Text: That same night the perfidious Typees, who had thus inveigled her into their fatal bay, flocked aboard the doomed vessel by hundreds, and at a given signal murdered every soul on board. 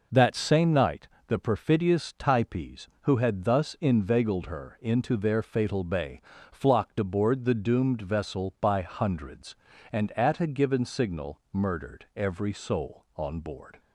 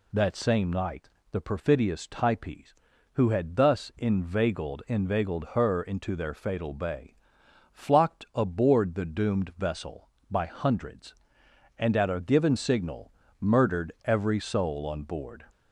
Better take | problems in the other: first | pauses between "night" and "the"; slight; at 1.0 s; 0.24 s long; slight in the first // says "inveigled" twice; at 4.8 s // pauses between "signal" and "murdered"; slight; at 13.1 s; 0.28 s long

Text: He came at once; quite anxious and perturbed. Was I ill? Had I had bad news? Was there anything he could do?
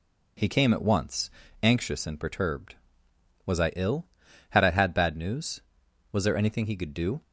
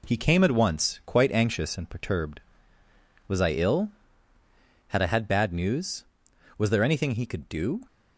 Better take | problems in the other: second | skips "quite"; at 1.4 s

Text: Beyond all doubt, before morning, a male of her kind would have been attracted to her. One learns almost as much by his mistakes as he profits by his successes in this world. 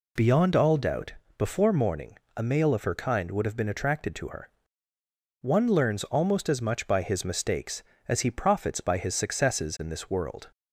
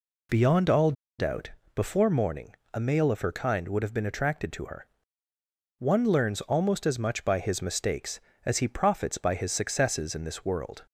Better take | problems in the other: first | pauses between "all" and "doubt"; slight; at 0.9 s; 0.26 s long

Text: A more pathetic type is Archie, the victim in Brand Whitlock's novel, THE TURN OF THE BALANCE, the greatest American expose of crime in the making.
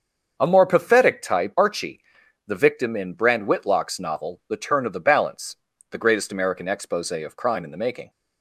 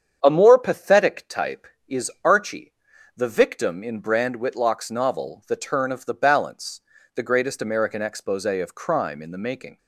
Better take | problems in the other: second | starts louder than the rest; until 1.4 s; 6.5 dB; strong in the second // skips "is"; at 1.5 s

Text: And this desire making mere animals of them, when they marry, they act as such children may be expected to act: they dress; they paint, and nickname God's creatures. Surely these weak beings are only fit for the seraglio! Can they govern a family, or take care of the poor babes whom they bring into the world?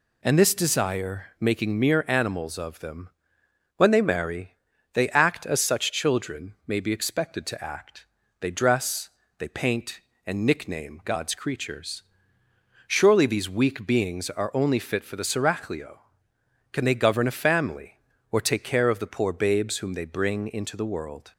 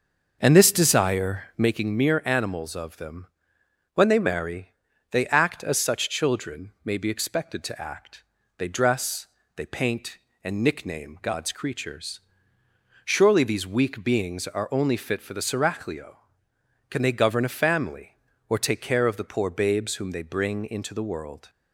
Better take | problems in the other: first | starts louder than the rest; until 1.7 s; 6 dB

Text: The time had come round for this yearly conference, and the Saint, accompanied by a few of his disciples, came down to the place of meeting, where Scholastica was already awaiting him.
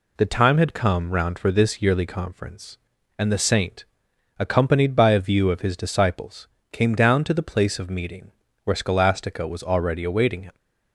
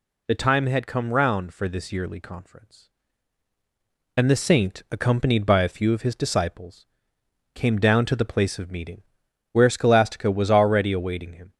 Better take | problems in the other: second | says "view" for "few"; at 5.1 s

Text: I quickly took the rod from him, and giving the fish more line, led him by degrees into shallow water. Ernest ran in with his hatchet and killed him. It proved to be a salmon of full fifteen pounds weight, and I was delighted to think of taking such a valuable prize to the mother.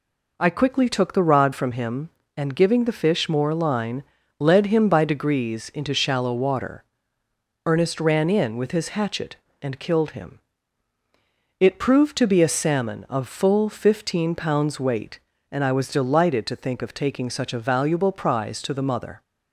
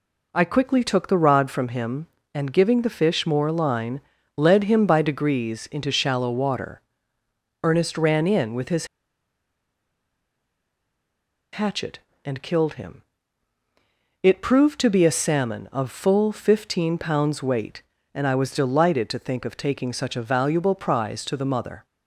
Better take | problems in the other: first | pauses between "his" and "hatchet"; strong; at 8.8 s; 2.6 s long

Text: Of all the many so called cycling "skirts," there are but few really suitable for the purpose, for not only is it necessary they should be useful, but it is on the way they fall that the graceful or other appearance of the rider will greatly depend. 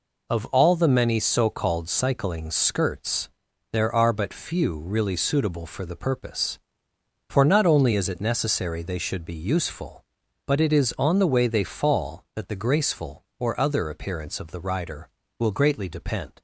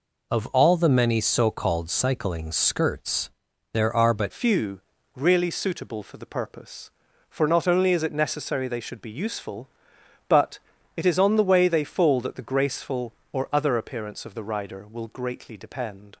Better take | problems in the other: first | changes voice at "few"; from 4.3 s on; 11.8 s long // pauses between "few" and "really"; slight; at 4.7 s; 0.36 s long // pauses between "but" and "it"; at 10.5 s; 0.40 s long

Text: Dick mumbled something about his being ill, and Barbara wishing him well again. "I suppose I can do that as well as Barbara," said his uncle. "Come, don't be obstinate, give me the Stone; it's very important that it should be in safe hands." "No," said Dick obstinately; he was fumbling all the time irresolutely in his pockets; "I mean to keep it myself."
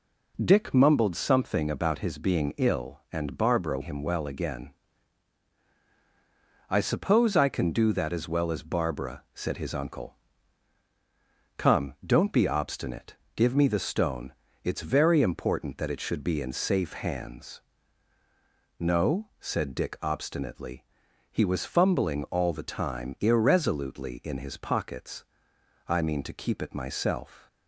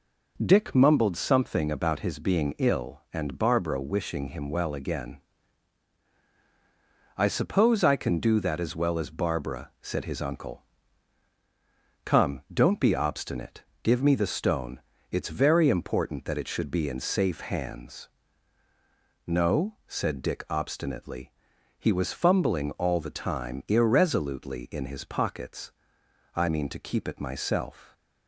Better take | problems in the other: second | skips "wishing"; at 3.8 s

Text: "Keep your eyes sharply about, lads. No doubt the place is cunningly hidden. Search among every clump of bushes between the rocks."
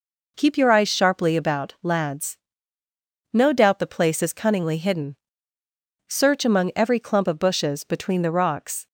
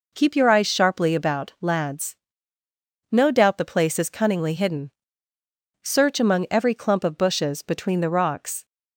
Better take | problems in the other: neither | none

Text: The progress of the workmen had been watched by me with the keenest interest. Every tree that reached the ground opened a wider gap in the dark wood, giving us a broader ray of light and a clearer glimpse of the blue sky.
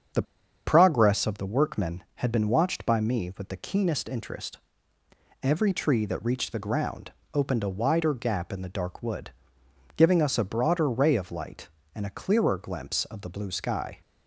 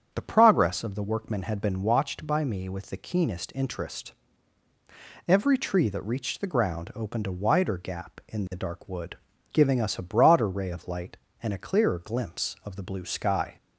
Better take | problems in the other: second | starts louder than the rest; strong; until 1.5 s; 7 dB; strong in the second // pauses between "The" and "progress"; at 0.2 s; 0.42 s long // pauses between "ground" and "opened"; slight; at 7.1 s; 0.22 s long

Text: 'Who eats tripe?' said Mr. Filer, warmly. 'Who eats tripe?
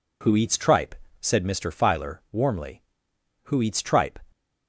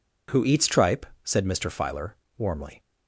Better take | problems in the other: first | stops before "Who eats tripe"; at 2.8 s

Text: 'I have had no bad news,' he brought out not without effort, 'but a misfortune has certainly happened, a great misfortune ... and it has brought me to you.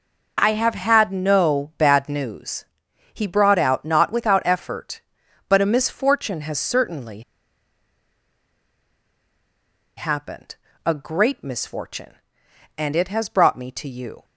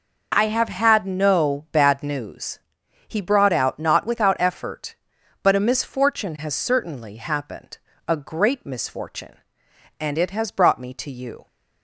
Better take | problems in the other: second | pauses between "certainly" and "happened"; strong; at 7.1 s; 2.7 s long

